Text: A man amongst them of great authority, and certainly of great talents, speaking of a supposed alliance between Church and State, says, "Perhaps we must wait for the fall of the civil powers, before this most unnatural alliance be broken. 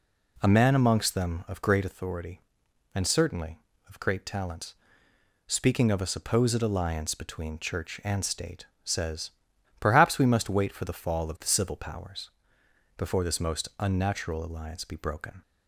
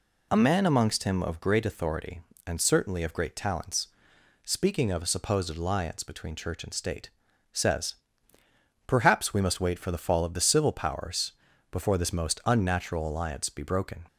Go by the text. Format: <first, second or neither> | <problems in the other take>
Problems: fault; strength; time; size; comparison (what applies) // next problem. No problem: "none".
first | says "him" for "them"; at 1.0 s